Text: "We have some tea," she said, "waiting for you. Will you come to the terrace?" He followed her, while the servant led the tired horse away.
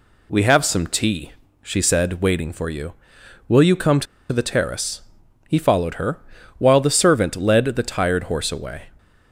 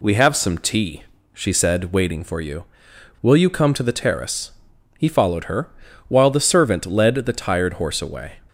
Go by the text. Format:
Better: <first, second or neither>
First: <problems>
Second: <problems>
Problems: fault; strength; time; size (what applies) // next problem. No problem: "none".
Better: second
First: pauses between "to" and "the"; slight; at 4.0 s; 0.26 s long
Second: none